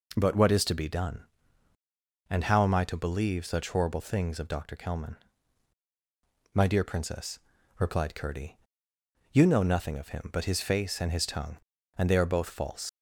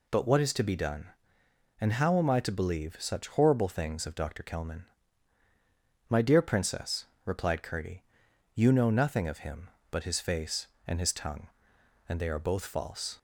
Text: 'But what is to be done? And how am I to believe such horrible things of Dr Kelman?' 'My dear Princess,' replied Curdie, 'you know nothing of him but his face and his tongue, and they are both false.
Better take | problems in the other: second | leaves "false" unfinished; at 12.8 s; 105 ms

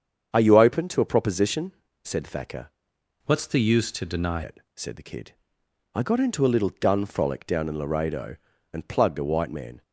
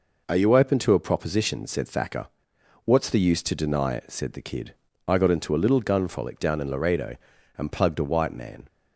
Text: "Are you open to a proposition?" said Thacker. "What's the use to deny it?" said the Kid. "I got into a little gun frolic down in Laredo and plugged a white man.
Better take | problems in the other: second | starts louder than the rest; strong; until 1.3 s; 7.5 dB // changes voice from "What's" to "deny"; from 3.2 to 4.4 s; 1.2 s long

